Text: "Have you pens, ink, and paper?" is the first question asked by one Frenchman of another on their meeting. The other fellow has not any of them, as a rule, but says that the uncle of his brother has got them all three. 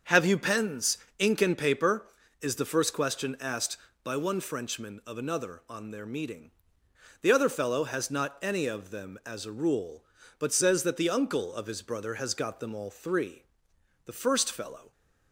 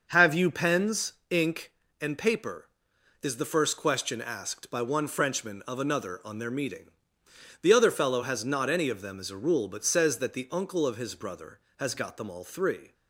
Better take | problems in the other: second | starts louder than the rest; until 1.2 s; 7 dB; also in the second // goes on to say "The first fellow"; noticeable; from 14.0 s on; 0.88 s long

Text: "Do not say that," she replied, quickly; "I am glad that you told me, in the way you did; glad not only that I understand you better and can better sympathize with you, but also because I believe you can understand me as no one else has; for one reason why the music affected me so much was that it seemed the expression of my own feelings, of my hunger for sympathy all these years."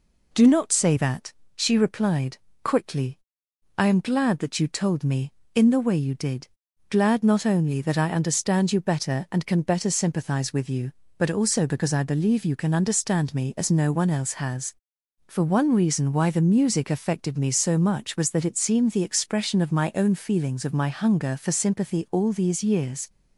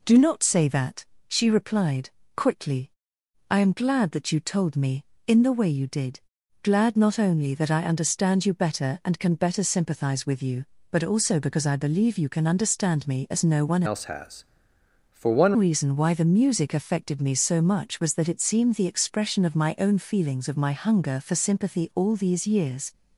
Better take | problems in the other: first | changes voice from "else" to "one"; from 13.8 to 15.5 s; 1.7 s long

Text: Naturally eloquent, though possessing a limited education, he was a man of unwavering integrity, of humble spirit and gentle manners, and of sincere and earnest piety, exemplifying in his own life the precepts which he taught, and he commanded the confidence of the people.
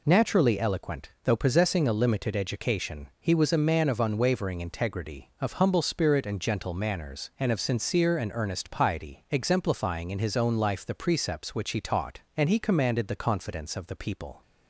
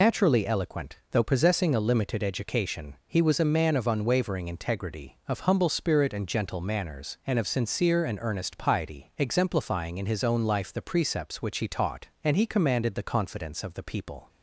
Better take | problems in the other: first | loses the start of "Naturally"; at 0.0 s; 80 ms

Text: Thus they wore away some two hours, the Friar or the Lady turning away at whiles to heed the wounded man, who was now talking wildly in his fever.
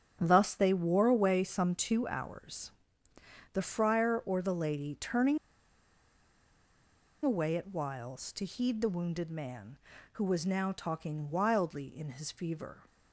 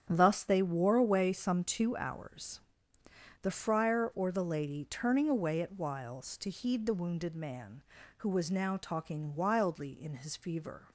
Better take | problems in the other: second | starts louder than the rest; strong; until 1.2 s; 8.5 dB; strong in the second // pauses between "turning" and "away"; strong; at 5.3 s; 1.8 s long

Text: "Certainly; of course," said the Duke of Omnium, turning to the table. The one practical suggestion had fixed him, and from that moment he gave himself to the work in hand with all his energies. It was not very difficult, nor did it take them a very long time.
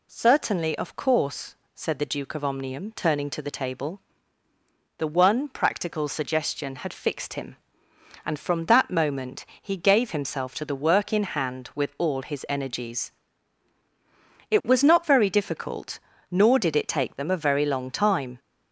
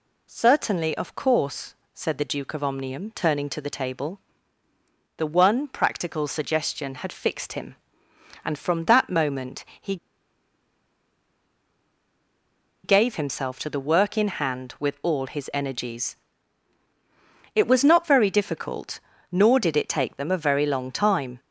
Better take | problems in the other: first | pauses between "moment" and "he"; slight; at 9.6 s; 0.16 s long; slight in the first // pauses between "he" and "gave"; strong; at 9.9 s; 2.8 s long

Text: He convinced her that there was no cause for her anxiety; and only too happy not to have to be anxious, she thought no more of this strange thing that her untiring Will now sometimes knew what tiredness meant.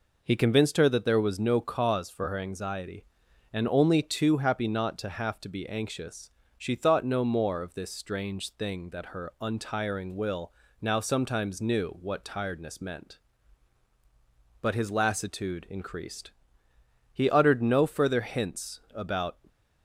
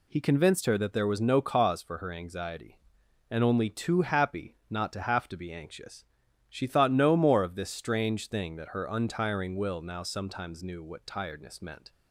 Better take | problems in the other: second | pauses between "Will" and "now"; slight; at 10.4 s; 0.30 s long // goes on to say "But his lassitude increased He uttered no further hints about"; strong; from 14.6 s on; 4.7 s long

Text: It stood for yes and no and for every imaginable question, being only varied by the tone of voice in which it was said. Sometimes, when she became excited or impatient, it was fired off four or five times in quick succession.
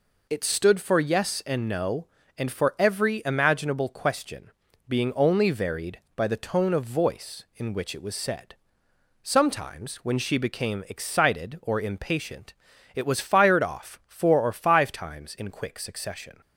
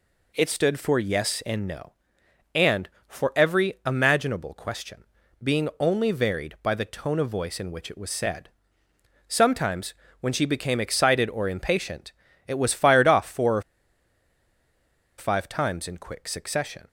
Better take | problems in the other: first | pauses between "or" and "five"; strong; at 13.6 s; 1.5 s long

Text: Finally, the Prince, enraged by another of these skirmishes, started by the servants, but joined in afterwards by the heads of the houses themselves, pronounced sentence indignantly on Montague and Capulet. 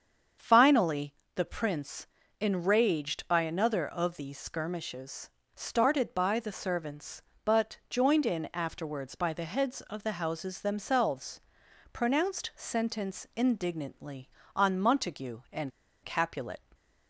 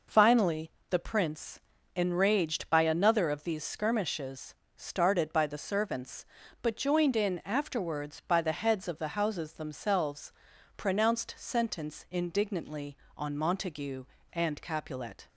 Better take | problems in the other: second | starts louder than the rest; strong; until 1.6 s; 7 dB // pauses between "and" and "Capulet"; slight; at 15.7 s; 0.33 s long

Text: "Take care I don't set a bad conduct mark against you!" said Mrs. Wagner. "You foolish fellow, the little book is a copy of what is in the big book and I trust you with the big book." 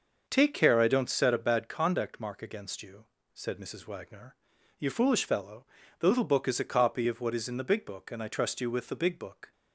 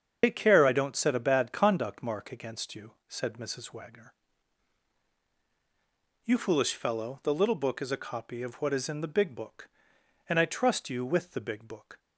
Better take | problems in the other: first | loses the start of "Take"; at 0.2 s; 90 ms // starts louder than the rest; strong; until 1.2 s; 7 dB; also in the first

